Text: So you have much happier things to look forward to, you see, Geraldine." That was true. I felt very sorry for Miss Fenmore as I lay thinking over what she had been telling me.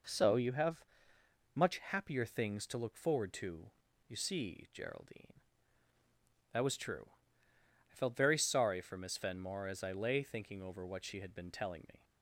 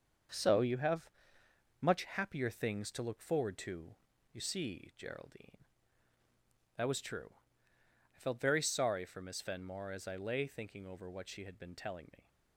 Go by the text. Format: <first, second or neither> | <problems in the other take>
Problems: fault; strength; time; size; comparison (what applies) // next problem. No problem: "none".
first | gets quieter; throughout; 6.5 dB // pauses between "have" and "much"; noticeable; at 1.1 s; 0.72 s long; noticeable in the first